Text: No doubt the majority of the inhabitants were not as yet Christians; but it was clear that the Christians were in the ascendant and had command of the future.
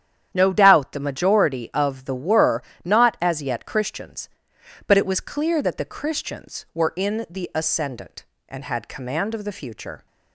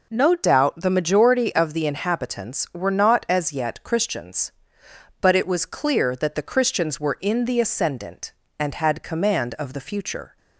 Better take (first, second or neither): second